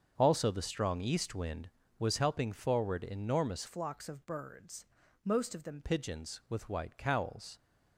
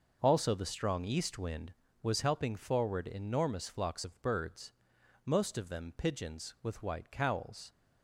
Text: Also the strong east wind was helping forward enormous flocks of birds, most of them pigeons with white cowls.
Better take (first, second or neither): second